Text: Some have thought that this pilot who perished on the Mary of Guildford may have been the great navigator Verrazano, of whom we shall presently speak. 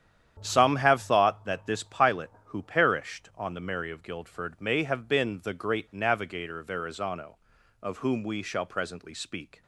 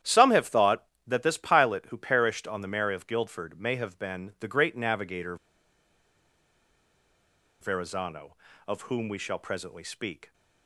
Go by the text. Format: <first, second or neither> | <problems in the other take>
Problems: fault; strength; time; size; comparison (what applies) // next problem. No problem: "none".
first | starts louder than the rest; strong; until 1.2 s; 11 dB; strong in the first // pauses between "navigator" and "Verrazano"; strong; at 5.3 s; 2.2 s long